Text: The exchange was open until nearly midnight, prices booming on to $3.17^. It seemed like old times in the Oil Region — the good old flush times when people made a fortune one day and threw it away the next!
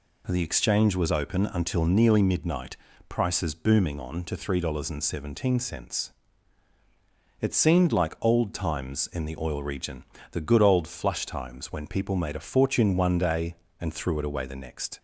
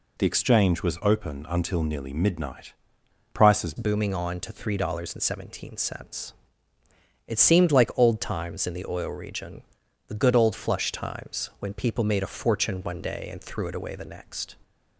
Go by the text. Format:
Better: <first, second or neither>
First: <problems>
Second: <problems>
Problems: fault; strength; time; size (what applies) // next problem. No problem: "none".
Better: first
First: none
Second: changes voice at "booming"; from 3.7 s on; 10.8 s long